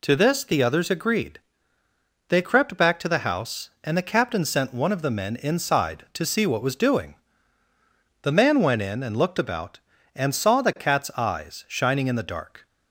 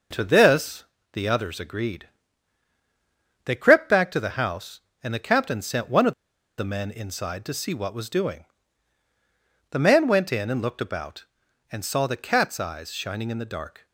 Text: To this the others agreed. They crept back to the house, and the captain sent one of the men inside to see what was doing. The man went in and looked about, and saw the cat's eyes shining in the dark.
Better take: first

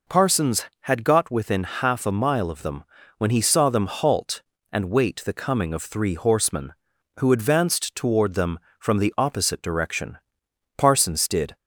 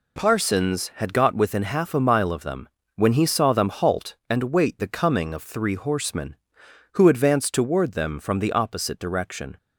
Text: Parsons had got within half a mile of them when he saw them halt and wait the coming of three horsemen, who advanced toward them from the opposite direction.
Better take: second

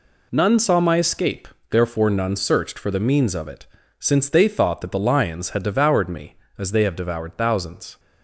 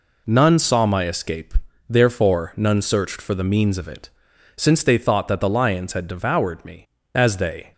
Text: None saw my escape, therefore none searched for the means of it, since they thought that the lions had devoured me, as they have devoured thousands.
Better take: first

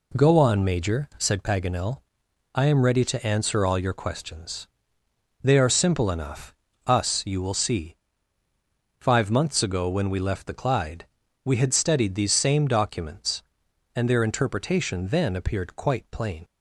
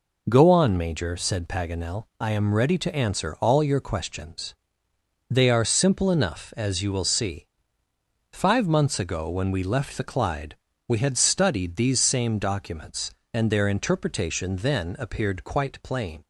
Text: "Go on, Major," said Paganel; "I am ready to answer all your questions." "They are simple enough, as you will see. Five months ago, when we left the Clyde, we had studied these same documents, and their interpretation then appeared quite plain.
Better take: second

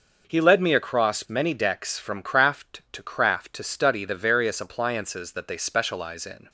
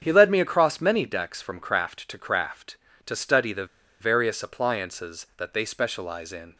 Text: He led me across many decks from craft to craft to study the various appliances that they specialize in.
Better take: first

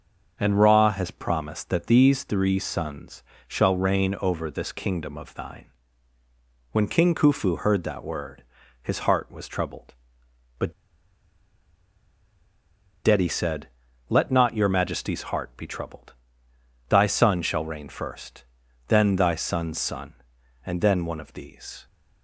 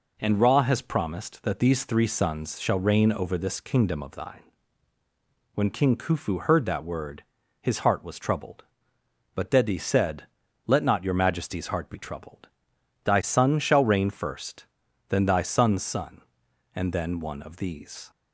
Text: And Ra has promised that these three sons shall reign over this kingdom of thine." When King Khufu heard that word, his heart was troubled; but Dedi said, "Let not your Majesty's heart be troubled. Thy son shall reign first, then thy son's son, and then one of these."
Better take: second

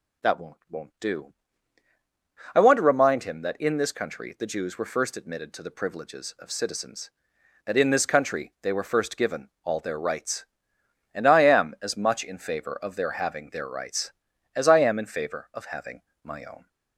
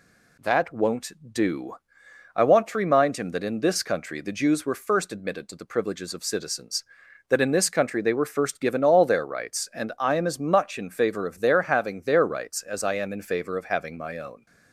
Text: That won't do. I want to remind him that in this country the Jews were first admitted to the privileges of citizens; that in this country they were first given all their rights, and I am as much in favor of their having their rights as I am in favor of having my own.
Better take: second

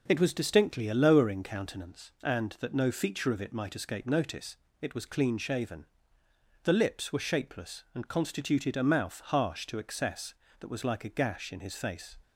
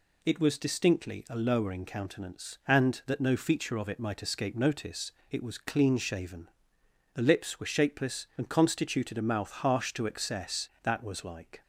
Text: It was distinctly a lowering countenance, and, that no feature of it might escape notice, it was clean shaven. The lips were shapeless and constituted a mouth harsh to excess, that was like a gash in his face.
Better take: first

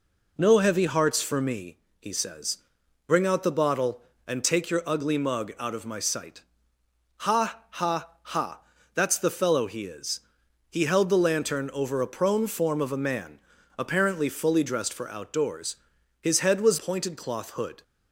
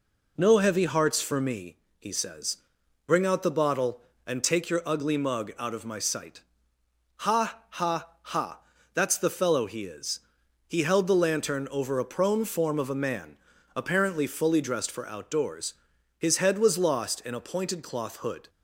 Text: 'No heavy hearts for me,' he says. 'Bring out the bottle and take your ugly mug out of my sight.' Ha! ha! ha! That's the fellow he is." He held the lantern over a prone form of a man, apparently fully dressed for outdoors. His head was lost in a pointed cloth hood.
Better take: second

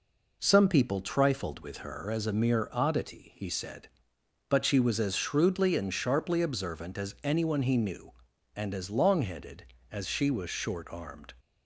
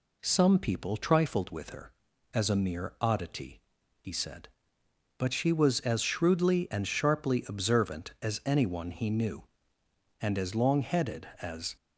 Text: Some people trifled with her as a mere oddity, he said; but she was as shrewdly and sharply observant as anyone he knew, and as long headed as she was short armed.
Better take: first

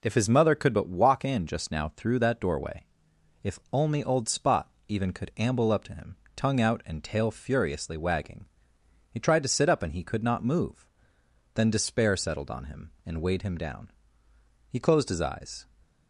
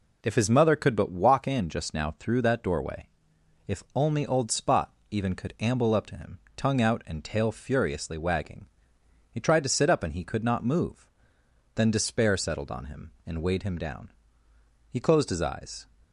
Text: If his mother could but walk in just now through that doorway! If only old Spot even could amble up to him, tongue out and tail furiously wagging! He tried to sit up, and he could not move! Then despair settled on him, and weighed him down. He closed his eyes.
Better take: neither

